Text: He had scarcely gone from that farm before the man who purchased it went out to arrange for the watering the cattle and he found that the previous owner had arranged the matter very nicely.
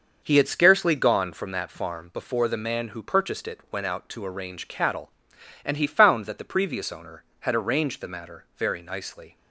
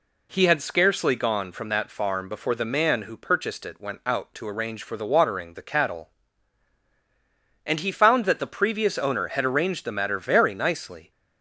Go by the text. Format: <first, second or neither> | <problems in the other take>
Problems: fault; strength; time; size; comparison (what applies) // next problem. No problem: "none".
second | starts louder than the rest; until 1.2 s; 6 dB // skips "for the watering the"; at 4.6 s